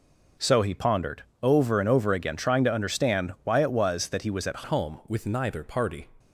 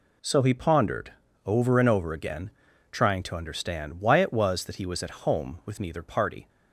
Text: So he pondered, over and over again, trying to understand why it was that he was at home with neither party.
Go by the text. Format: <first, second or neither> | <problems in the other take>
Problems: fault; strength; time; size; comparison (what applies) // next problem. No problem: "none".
second | changes voice at "home"; from 4.6 s on; 1.4 s long